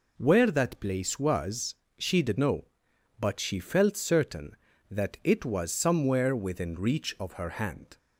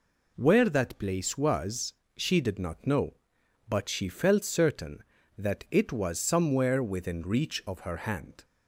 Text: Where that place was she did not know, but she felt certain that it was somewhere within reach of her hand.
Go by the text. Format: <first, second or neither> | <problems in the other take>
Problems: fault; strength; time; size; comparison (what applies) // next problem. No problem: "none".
second | pauses between "was" and "she"; slight; at 1.7 s; 0.24 s long; slight in the second // skips "not"; at 2.3 s